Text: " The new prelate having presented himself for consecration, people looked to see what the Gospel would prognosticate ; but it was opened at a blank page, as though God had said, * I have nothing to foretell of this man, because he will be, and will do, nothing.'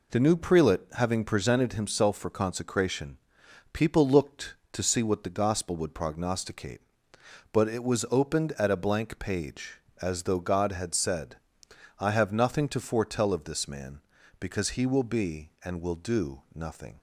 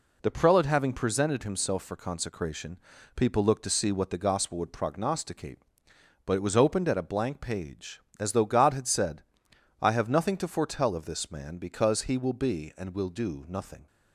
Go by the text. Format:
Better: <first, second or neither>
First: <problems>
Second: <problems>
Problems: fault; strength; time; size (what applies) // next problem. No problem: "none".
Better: first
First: none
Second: skips "new"; at 0.3 s